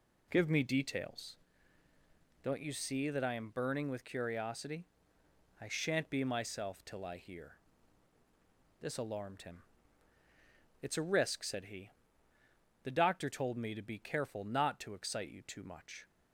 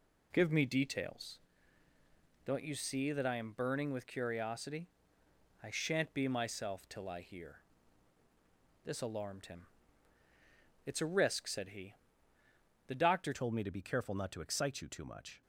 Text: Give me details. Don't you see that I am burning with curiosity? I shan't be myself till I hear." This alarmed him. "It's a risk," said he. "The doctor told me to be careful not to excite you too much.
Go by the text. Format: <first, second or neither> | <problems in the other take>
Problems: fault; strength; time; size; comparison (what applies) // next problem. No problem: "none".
first | changes voice at "told"; from 13.3 s on; 2.1 s long